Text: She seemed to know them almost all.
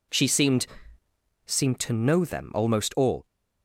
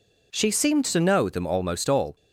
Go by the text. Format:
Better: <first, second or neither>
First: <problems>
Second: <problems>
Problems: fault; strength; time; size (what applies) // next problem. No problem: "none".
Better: second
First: says "seemed" twice; at 1.4 s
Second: none